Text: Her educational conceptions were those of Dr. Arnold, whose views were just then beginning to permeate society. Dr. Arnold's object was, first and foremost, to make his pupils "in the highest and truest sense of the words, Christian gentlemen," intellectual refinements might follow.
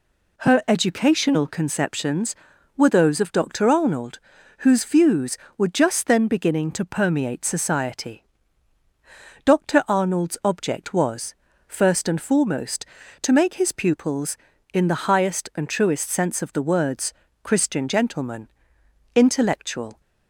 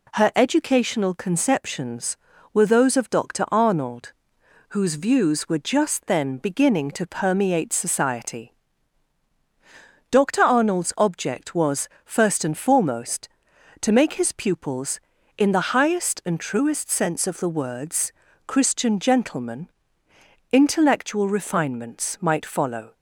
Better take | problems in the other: second | stops before "refinements might follow"; at 19.9 s

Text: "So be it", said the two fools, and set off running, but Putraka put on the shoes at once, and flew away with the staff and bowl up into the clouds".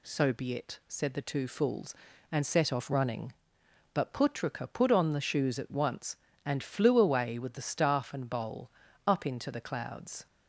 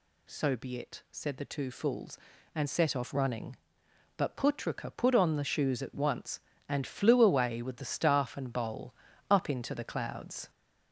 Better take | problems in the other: first | gets louder; noticeable; throughout; 4 dB // pauses between "bowl" and "up"; slight; at 8.9 s; 0.36 s long; slight in the first

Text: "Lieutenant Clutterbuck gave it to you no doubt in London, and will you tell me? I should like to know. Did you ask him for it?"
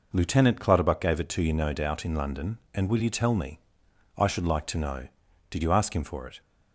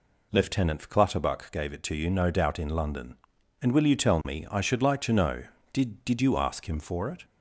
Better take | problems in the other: first | says "Did" twice; at 6.0 s

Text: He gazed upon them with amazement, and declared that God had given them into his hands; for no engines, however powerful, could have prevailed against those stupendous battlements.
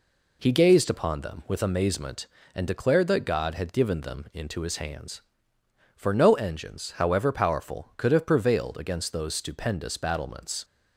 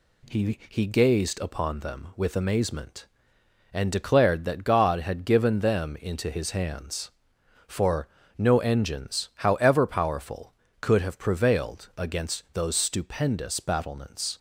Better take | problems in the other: first | says "He" twice; at 0.6 s // pauses between "for" and "no"; slight; at 8.0 s; 0.30 s long

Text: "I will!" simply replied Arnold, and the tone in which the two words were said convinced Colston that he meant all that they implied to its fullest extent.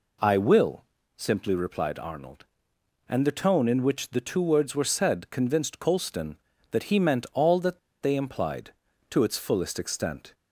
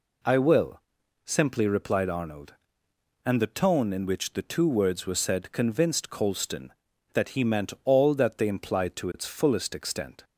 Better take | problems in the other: second | pauses between "that" and "they"; slight; at 7.7 s; 0.22 s long

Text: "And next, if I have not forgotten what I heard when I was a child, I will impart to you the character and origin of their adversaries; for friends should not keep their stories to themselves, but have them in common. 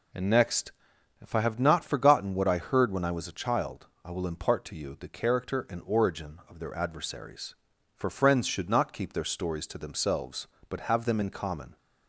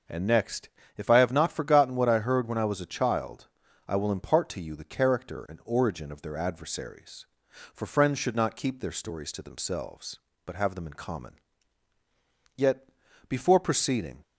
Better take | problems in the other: first | starts louder than the rest; noticeable; until 1.3 s; 6 dB // goes on to say "Yet before proceeding"; from 12.5 s on; 1.6 s long

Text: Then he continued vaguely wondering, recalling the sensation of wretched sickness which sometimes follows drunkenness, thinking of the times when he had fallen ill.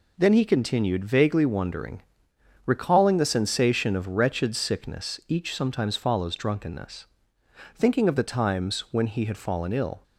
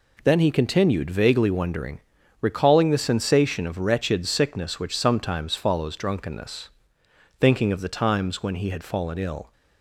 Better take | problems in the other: second | says "each" for "which"; at 5.2 s

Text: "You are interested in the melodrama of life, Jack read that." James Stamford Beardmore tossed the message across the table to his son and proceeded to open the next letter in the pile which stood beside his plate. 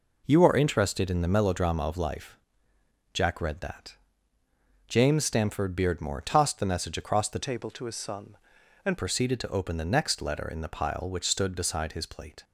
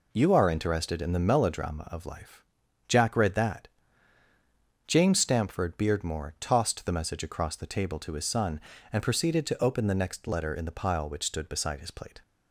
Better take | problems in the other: second | changes voice from "table" to "and"; from 7.3 to 8.9 s; 1.6 s long

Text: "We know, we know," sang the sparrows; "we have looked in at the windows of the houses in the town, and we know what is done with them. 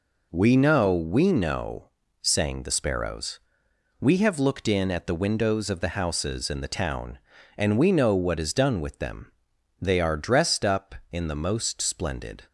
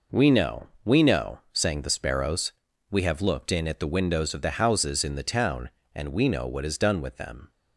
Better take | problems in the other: second | goes on to say "They are dressed up in the most splendid"; strong; from 9.8 s on; 2.6 s long

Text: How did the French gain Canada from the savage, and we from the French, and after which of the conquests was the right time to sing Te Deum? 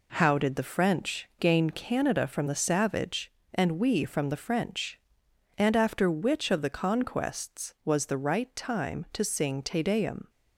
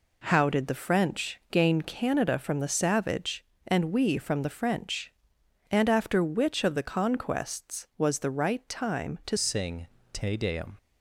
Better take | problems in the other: first | changes voice at "sing"; from 9.3 s on; 1.4 s long // pauses between "sing" and "Te"; slight; at 9.8 s; 0.26 s long

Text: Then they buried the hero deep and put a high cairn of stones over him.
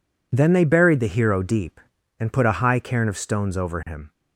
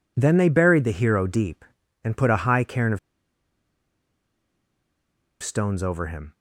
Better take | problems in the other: first | pauses between "of" and "stones"; strong; at 2.9 s; 2.4 s long

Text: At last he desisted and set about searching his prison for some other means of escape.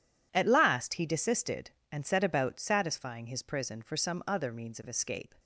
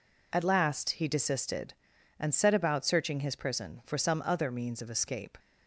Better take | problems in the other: second | says "satisfying" for "searching"; at 2.5 s

